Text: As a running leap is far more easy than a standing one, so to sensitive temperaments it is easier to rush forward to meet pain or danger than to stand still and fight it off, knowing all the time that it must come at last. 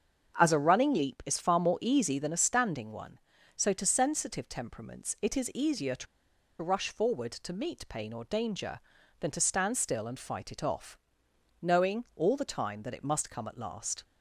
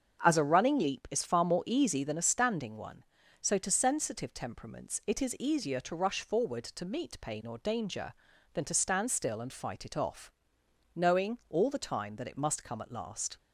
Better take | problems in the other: second | starts louder than the rest; until 1.4 s; 7 dB; also in the second // pauses between "to" and "rush"; noticeable; at 6.0 s; 0.55 s long

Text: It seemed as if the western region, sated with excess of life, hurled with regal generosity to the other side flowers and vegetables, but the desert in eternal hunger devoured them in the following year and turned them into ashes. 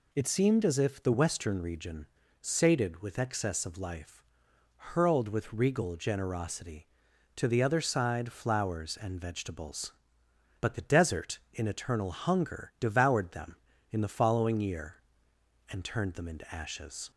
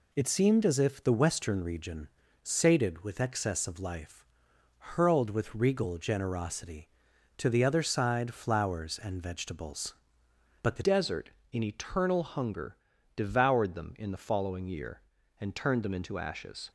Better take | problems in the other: first | changes voice at "desert"; from 10.8 s on; 5.9 s long // pauses between "hunger" and "devoured"; at 12.7 s; 0.40 s long

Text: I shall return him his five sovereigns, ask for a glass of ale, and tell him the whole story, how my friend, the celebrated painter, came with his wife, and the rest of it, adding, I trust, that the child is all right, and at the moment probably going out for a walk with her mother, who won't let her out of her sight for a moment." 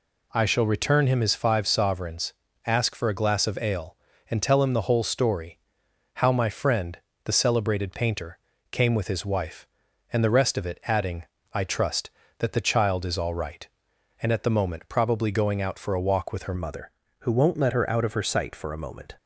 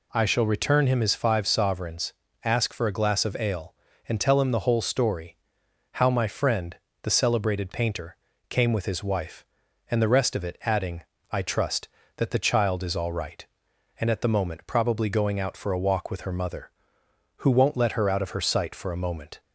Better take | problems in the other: second | changes voice at "mother"; from 16.5 s on; 2.6 s long

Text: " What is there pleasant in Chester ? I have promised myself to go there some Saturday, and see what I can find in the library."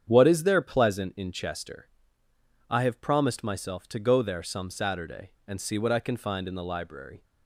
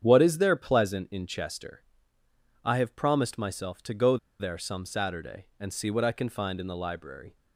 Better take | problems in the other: first | starts louder than the rest; strong; until 1.0 s; 8.5 dB; strong in the first // pauses between "go" and "there"; slight; at 4.1 s; 0.22 s long

